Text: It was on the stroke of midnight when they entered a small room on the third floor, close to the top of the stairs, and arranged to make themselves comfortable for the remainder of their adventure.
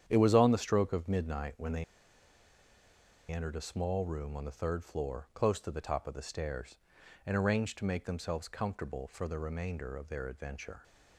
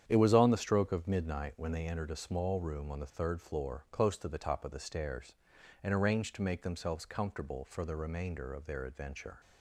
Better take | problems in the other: second | starts louder than the rest; strong; until 1.0 s; 9 dB; strong in the second // pauses between "they" and "entered"; strong; at 1.8 s; 1.4 s long

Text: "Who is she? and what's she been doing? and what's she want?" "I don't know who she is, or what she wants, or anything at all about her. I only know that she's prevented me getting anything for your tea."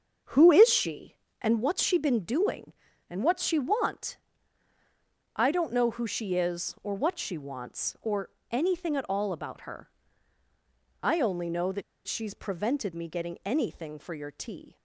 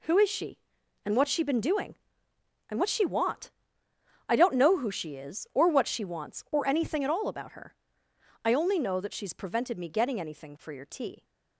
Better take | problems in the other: second | starts louder than the rest; until 1.5 s; 7 dB // pauses between "or" and "anything"; slight; at 8.2 s; 0.20 s long // pauses between "that" and "she's"; slight; at 11.8 s; 0.24 s long

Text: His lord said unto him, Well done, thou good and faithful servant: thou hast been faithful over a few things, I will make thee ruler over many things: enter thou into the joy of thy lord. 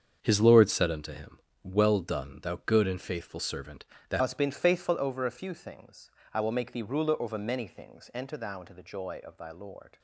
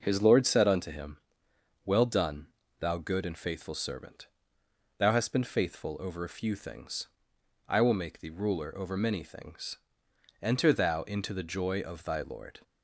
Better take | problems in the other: second | starts louder than the rest; strong; until 1.2 s; 7.5 dB // changes voice at "hast"; from 4.1 s on; 5.8 s long

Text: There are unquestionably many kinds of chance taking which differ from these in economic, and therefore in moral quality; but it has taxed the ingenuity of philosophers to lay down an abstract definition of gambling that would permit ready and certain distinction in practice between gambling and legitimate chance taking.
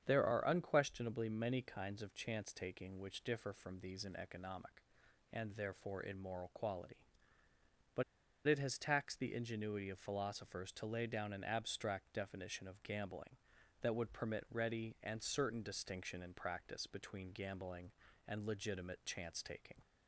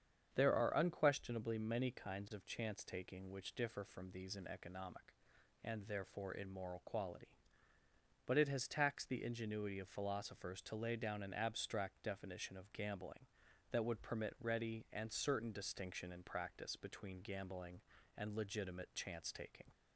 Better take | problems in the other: second | starts louder than the rest; strong; until 1.0 s; 8 dB; strong in the second // pauses between "but" and "it"; at 8.0 s; 0.42 s long

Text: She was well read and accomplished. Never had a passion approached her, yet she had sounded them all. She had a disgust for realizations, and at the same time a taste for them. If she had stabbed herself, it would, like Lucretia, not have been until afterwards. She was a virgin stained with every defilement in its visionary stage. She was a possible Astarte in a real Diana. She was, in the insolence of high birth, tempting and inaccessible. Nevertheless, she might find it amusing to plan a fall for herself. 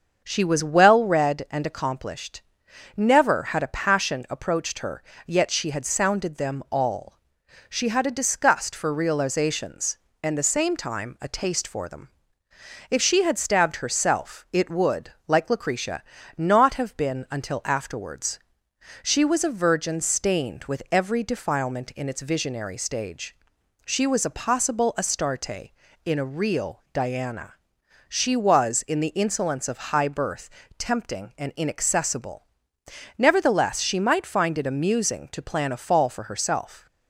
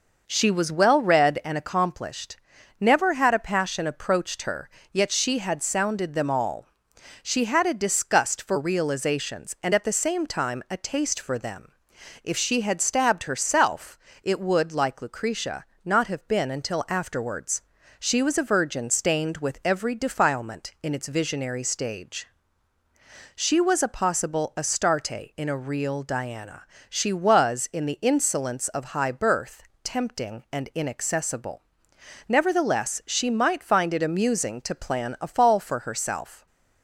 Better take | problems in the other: second | starts louder than the rest; until 1.2 s; 6.5 dB // skips "at"; at 10.3 s

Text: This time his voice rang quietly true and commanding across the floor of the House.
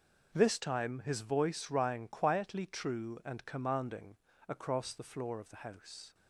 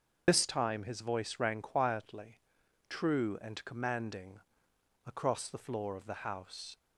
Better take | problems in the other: first | loses the start of "This"; at 0.2 s; 70 ms // starts louder than the rest; noticeable; until 1.2 s; 6 dB // pauses between "quietly" and "true"; noticeable; at 2.3 s; 0.50 s long // pauses between "commanding" and "across"; noticeable; at 4.3 s; 0.66 s long; slight in the first

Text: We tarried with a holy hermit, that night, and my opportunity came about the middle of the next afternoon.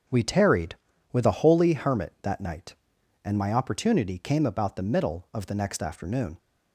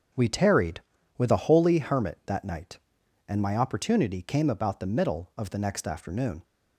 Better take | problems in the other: neither | starts louder than the rest; the same in both

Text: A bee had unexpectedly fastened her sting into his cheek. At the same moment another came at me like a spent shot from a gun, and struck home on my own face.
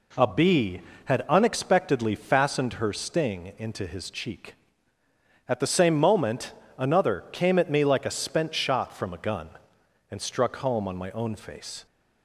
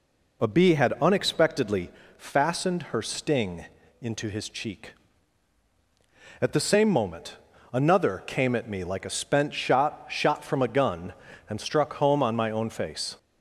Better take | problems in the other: first | pauses between "unexpectedly" and "fastened"; slight; at 1.9 s; 0.26 s long // pauses between "sting" and "into"; slight; at 3.6 s; 0.34 s long // pauses between "moment" and "another"; slight; at 7.3 s; 0.36 s long; slight in the first // says "shot" twice; at 10.0 s

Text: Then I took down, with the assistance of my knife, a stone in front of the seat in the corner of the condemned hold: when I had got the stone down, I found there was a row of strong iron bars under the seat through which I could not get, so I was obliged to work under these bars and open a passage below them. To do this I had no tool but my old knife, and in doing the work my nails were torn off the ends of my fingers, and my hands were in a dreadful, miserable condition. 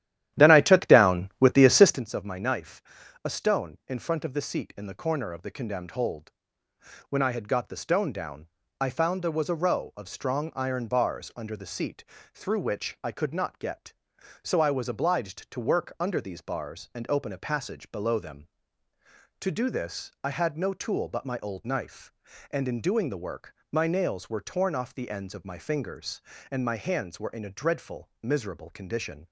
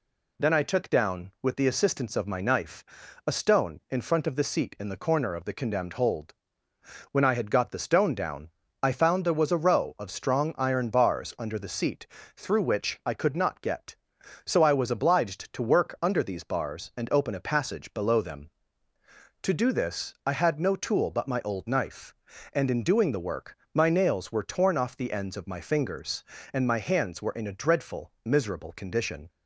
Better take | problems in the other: second | starts louder than the rest; strong; until 2.0 s; 12 dB // pauses between "seat" and "through"; slight; at 12.0 s; 0.30 s long; slight in the second // pauses between "work" and "my"; slight; at 23.5 s; 0.18 s long; slight in the second

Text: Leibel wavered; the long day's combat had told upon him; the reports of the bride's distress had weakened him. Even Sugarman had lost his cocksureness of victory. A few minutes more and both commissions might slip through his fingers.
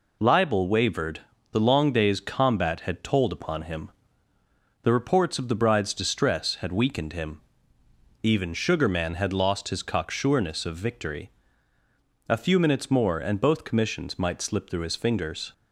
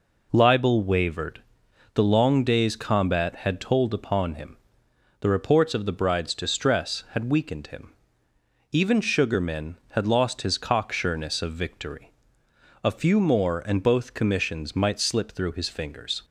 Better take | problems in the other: first | skips "minutes"; at 13.1 s

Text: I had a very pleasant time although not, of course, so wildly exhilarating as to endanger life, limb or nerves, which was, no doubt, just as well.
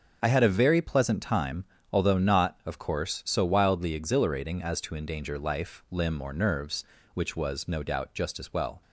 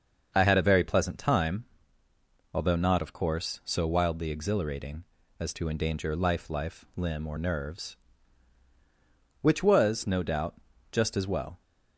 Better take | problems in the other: first | starts louder than the rest; until 1.3 s; 6.5 dB; also in the first // pauses between "time" and "although"; noticeable; at 1.6 s; 0.88 s long; slight in the first // says "life" twice; at 6.4 s

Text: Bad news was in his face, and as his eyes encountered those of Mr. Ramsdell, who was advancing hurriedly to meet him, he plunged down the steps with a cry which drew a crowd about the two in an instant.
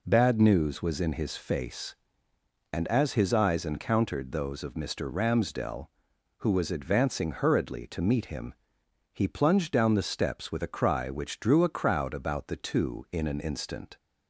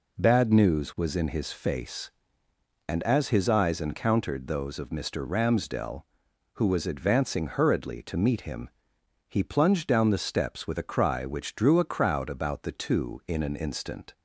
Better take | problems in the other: neither | none

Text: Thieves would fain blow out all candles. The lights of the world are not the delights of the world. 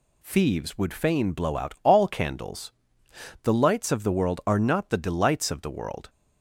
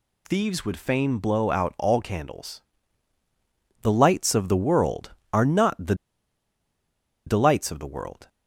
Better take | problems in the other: first | pauses between "the" and "delights"; strong; at 5.9 s; 1.3 s long

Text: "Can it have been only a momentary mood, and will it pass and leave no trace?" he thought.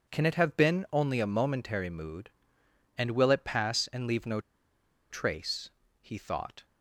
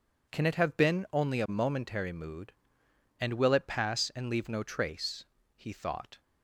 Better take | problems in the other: second | pauses between "no" and "trace"; noticeable; at 4.3 s; 0.70 s long

